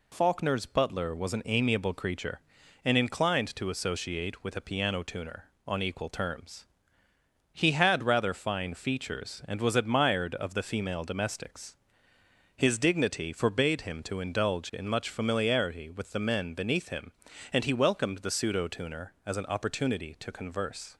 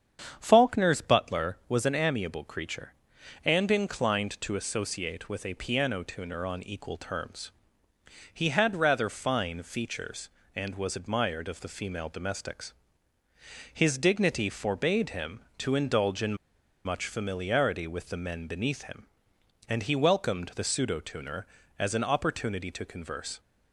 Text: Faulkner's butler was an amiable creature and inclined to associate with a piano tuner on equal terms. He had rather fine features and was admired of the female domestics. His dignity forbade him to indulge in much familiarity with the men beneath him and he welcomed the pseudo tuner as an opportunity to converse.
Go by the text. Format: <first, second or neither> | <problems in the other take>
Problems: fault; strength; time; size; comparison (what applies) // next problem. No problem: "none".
first | starts louder than the rest; strong; until 1.3 s; 8 dB // pauses between "in" and "much"; noticeable; at 16.3 s; 0.50 s long